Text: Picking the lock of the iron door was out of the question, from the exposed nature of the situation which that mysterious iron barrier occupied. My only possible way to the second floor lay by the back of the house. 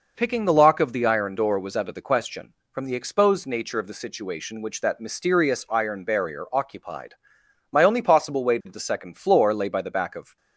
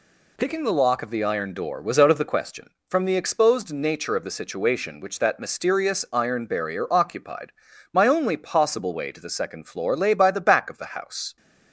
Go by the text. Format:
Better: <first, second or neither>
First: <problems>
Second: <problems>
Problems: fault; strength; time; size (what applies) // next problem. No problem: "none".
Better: second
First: stops before "the house"; at 10.3 s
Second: none